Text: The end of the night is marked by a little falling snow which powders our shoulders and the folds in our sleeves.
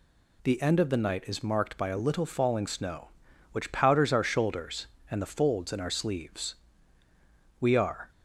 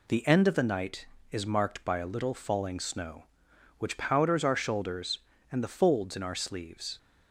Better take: second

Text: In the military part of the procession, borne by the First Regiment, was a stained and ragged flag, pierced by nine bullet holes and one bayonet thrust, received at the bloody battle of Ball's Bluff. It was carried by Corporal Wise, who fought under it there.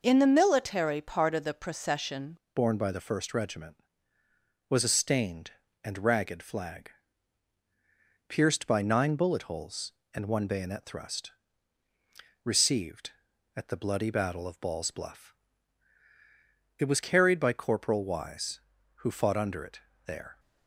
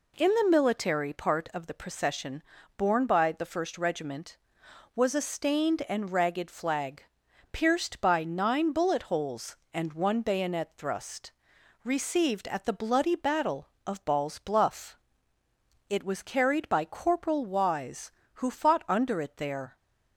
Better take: second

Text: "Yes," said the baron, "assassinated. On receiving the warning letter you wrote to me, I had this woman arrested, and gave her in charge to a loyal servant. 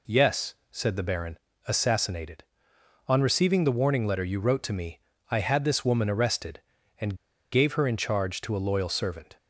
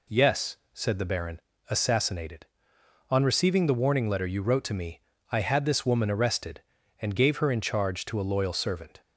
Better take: second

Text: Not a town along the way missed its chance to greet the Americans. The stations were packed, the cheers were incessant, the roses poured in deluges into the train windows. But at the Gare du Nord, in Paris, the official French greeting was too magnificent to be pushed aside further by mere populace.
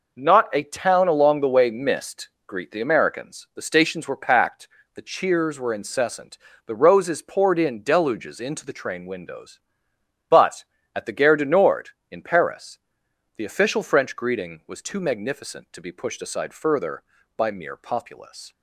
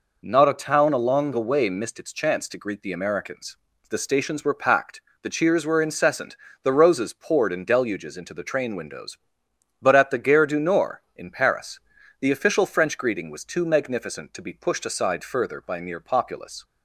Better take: second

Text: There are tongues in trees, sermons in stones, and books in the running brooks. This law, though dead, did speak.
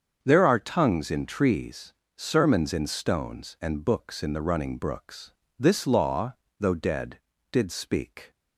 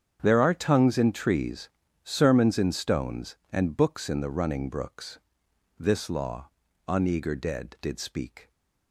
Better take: first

